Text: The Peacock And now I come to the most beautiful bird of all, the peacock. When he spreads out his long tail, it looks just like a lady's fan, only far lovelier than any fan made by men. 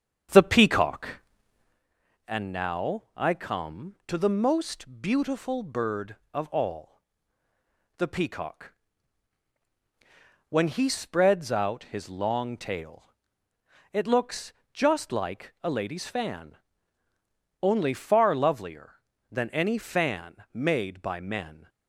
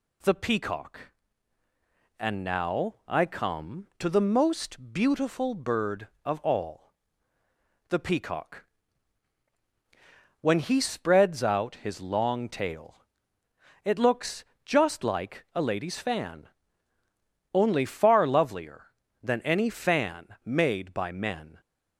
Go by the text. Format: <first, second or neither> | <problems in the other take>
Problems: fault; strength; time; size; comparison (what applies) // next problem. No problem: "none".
second | starts louder than the rest; strong; until 1.9 s; 8 dB // pauses between "looks" and "just"; slight; at 14.5 s; 0.18 s long; slight in the second // pauses between "fan" and "made"; slight; at 20.3 s; 0.18 s long; slight in the second